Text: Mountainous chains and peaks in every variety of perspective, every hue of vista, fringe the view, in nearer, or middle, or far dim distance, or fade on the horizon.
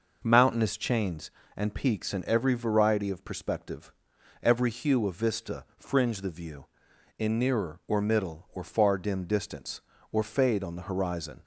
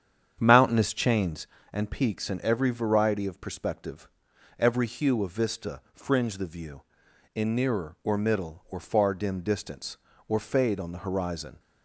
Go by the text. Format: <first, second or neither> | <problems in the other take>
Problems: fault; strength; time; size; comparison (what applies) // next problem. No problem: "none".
first | starts louder than the rest; strong; until 1.7 s; 8.5 dB